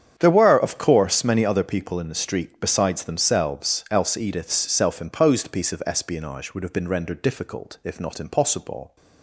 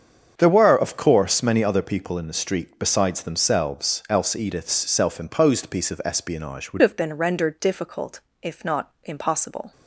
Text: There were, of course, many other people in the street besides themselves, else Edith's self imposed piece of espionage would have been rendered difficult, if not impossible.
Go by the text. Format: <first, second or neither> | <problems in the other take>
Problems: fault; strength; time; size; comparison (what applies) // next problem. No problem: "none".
first | starts louder than the rest; strong; until 1.3 s; 7.5 dB; strong in the first // changes voice at "have"; from 6.8 s on; 2.9 s long